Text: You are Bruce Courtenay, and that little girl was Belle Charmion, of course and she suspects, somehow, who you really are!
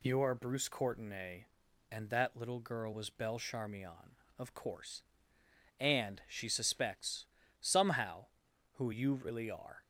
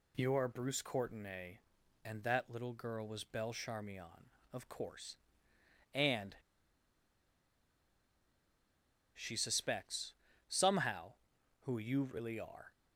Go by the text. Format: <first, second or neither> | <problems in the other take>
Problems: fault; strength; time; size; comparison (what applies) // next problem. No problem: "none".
first | pauses between "and" and "she"; strong; at 6.3 s; 2.7 s long